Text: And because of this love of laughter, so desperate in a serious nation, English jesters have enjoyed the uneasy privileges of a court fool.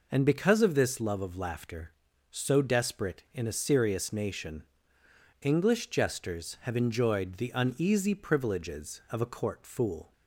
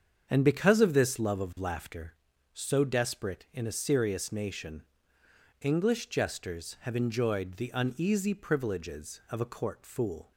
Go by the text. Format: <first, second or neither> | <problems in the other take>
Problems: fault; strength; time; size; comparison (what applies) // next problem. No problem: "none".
first | starts louder than the rest; strong; until 2.1 s; 7.5 dB